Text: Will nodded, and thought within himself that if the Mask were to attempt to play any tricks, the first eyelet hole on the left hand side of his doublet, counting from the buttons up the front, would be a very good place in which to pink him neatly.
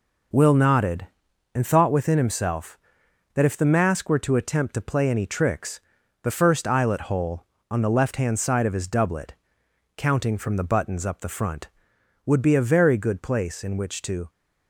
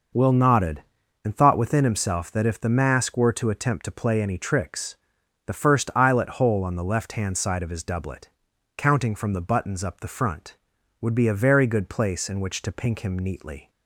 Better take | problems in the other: second | stops before "pink him neatly"; at 14.2 s

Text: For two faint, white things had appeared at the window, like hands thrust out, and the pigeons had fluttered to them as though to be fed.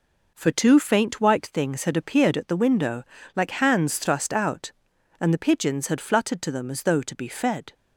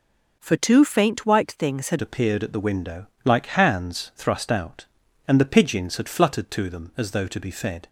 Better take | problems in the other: first | changes voice at "appeared"; from 1.9 s on; 5.9 s long

